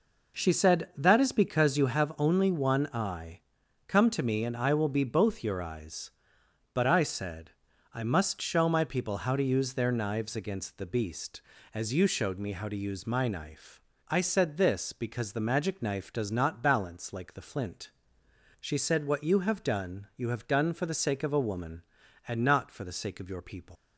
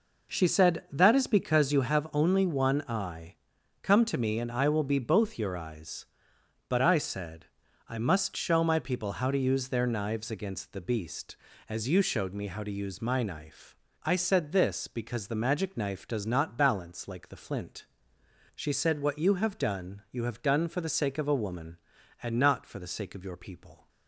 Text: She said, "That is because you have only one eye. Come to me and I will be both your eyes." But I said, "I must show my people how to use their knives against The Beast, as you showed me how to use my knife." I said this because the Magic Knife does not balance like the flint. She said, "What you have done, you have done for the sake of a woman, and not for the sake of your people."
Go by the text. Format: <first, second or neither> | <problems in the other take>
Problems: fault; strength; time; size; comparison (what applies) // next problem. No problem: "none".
second | leaves "people" unfinished; at 23.7 s; 180 ms